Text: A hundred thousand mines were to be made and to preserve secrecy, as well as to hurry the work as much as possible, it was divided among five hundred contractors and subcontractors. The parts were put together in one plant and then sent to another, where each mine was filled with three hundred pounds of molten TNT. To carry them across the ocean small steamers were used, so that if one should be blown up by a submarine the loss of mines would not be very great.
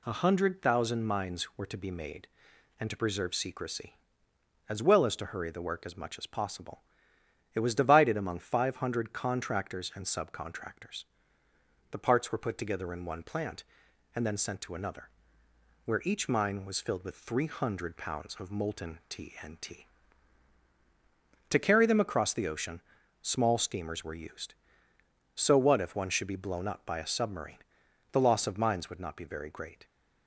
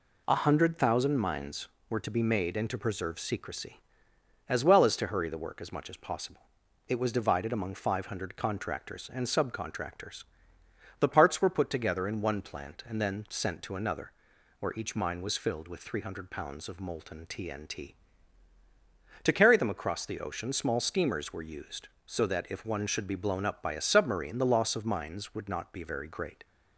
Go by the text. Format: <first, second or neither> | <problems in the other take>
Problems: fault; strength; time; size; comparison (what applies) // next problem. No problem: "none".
second | pauses between "ocean" and "small"; at 22.8 s; 0.40 s long // says "what" for "that"; at 25.5 s // pauses between "submarine" and "the"; noticeable; at 27.5 s; 0.54 s long